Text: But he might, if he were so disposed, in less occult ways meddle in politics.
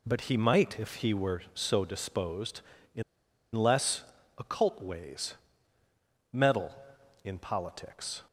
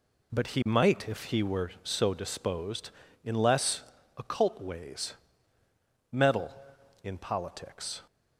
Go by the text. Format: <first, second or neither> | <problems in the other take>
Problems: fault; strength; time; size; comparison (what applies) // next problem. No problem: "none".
second | pauses between "in" and "less"; noticeable; at 3.0 s; 0.51 s long // pauses between "less" and "occult"; slight; at 4.0 s; 0.34 s long; slight in the second // pauses between "ways" and "meddle"; noticeable; at 5.3 s; 0.98 s long; noticeable in the second